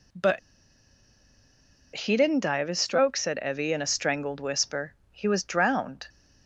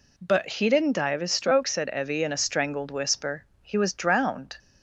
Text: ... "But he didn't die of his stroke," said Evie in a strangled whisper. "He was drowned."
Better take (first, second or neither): second